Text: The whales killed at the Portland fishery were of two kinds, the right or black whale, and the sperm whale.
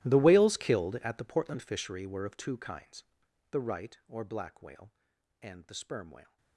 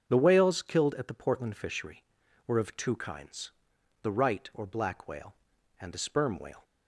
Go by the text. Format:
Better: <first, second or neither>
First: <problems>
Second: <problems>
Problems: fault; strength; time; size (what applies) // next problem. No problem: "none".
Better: second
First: gets quieter; strong; throughout; 22 dB // starts louder than the rest; strong; until 1.1 s; 15.5 dB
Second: starts louder than the rest; until 1.1 s; 7 dB